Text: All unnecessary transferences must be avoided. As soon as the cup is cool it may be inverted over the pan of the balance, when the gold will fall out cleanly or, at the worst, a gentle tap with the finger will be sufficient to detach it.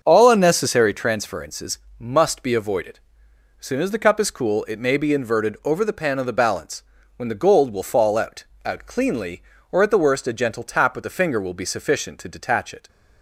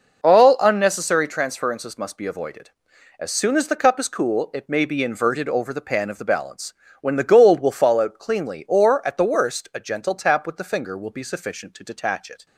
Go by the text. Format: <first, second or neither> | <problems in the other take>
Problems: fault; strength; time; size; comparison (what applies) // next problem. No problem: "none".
second | starts louder than the rest; until 1.0 s; 6.5 dB // pauses between "transferences" and "must"; slight; at 1.7 s; 0.22 s long // says "out" twice; at 8.6 s